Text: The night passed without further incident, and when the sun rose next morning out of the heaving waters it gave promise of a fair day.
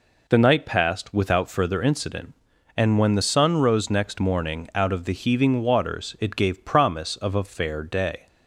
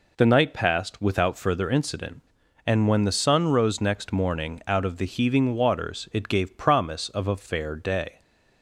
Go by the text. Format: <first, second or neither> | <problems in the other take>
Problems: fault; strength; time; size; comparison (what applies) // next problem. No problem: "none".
neither | none